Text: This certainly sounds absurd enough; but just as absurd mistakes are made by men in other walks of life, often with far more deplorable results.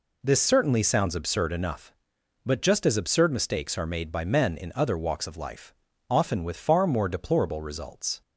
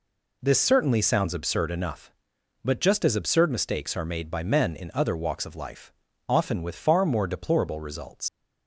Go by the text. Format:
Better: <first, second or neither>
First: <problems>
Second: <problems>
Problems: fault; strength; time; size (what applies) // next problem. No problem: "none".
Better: first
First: none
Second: leaves "results" unfinished; at 8.2 s; 115 ms